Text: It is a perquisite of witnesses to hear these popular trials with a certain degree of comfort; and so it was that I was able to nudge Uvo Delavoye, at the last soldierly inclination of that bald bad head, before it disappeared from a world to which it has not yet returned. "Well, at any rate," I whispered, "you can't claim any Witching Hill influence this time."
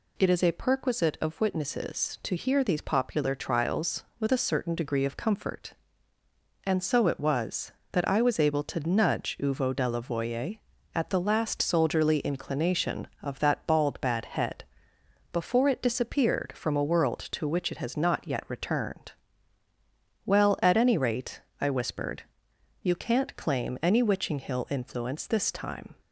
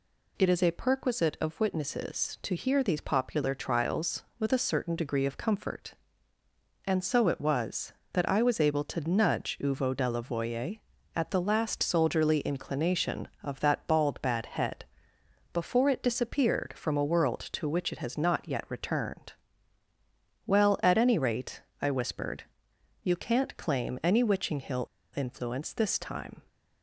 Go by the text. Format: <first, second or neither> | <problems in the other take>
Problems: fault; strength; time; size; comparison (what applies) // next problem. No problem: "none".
first | pauses between "Hill" and "influence"; slight; at 24.8 s; 0.29 s long